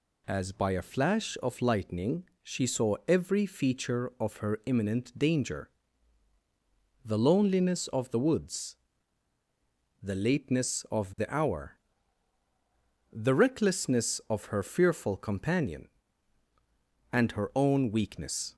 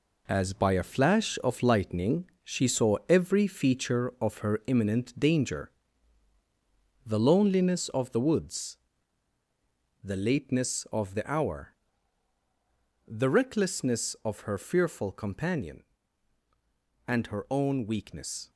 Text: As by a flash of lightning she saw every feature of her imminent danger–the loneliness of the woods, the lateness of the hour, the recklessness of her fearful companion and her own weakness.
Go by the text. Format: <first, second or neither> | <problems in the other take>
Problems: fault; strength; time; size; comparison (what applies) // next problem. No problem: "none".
first | gets quieter; strong; throughout; 7.5 dB // pauses between "lightning" and "she"; slight; at 2.2 s; 0.18 s long; slight in the first